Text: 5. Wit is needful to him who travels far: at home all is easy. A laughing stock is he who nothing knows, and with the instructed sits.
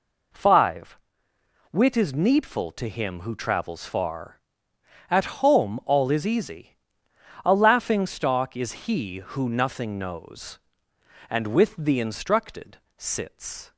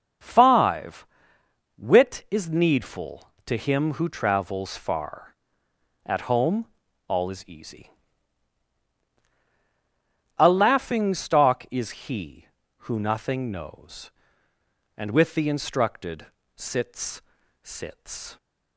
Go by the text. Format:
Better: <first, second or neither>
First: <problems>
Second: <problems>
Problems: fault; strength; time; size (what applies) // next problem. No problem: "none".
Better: first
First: pauses between "instructed" and "sits"; slight; at 12.7 s; 0.20 s long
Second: pauses between "home" and "all"; at 6.6 s; 0.42 s long // pauses between "instructed" and "sits"; slight; at 16.2 s; 0.28 s long // says "sits" twice; at 17.6 s